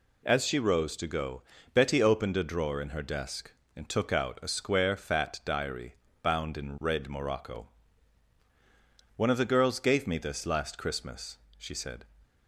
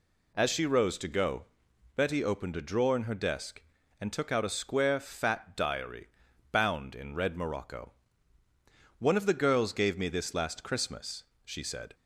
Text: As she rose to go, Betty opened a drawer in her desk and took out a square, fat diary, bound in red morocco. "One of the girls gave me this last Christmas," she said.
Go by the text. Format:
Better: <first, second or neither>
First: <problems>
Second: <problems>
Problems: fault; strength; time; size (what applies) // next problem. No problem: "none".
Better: neither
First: none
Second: none